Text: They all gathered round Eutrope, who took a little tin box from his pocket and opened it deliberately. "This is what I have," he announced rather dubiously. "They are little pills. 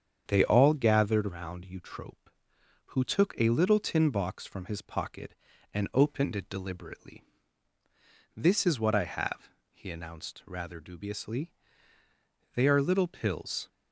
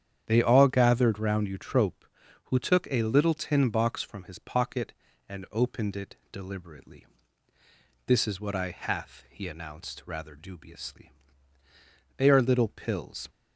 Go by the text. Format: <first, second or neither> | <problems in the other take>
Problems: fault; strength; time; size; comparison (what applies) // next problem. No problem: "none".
first | starts louder than the rest; strong; until 1.2 s; 9 dB; strong in the first // pauses between "it" and "deliberately"; slight; at 6.1 s; 0.16 s long // says "hath" for "have"; at 8.7 s